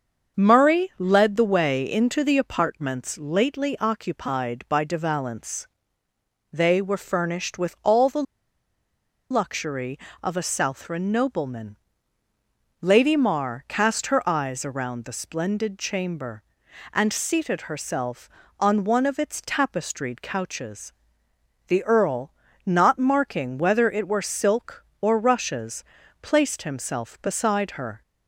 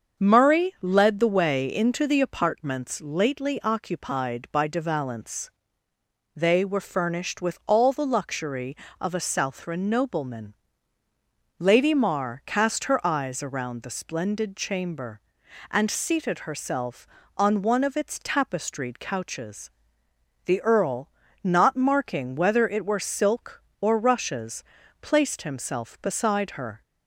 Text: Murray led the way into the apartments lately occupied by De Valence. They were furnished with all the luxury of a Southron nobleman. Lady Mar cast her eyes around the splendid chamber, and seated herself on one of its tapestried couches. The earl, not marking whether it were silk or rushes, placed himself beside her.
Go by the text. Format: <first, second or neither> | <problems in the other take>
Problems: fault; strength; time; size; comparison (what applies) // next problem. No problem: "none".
second | starts louder than the rest; until 1.4 s; 7 dB; also in the second // pauses between "the" and "luxury"; at 8.2 s; 1.0 s long